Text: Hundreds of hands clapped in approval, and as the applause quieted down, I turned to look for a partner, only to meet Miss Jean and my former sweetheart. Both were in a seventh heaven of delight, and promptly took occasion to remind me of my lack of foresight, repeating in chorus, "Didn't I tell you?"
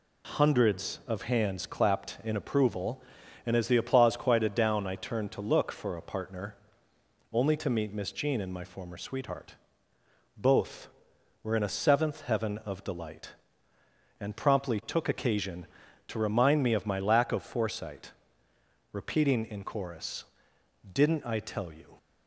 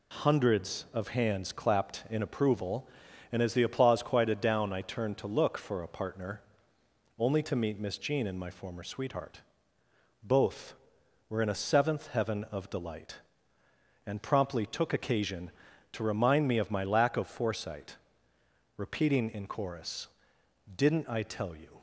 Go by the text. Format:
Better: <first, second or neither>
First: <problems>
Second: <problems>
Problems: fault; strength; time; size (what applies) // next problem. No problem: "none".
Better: neither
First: none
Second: none